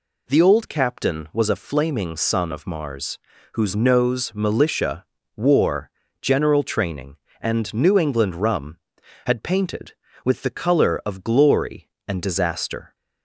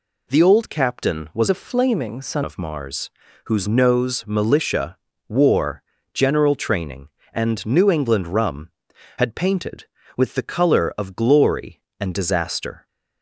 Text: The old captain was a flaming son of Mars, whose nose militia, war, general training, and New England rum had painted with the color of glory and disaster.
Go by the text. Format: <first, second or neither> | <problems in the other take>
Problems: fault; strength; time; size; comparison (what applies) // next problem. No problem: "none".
first | changes voice from "a" to "son"; from 1.5 to 2.4 s; 0.9 s long